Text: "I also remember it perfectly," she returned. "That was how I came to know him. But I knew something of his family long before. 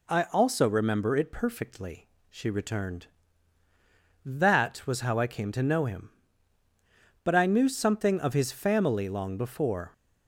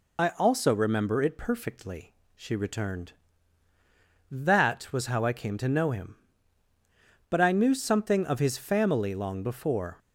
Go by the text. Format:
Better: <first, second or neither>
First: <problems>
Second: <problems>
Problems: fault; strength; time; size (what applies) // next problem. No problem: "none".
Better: first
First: none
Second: loses the start of "I"; at 0.1 s; 45 ms